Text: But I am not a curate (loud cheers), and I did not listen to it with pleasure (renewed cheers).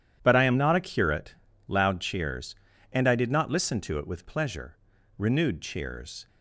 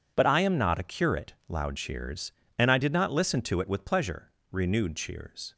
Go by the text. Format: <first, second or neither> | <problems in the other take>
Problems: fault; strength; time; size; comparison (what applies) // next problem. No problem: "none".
neither | none